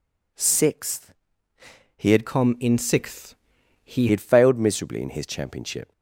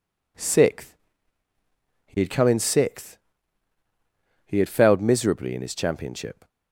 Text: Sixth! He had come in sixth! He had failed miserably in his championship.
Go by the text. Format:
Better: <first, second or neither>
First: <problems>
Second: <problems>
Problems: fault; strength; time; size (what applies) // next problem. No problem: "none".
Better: second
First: changes voice from "come" to "He"; from 2.2 to 4.0 s; 1.8 s long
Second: none